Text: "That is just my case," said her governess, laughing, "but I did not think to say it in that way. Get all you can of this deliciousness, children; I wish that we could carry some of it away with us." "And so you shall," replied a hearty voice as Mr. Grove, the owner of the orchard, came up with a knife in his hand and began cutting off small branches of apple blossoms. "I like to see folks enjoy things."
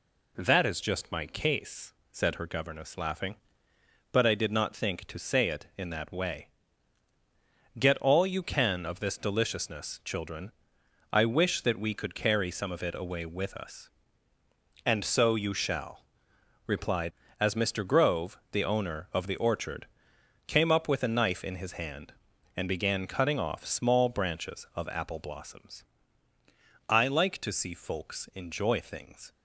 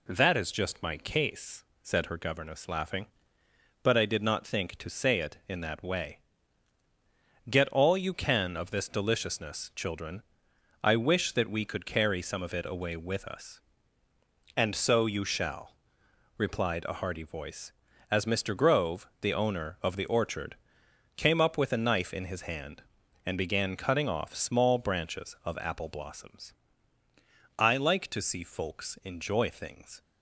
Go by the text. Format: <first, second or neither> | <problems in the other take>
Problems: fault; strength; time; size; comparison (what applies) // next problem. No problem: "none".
second | skips "a hearty voice"; at 17.2 s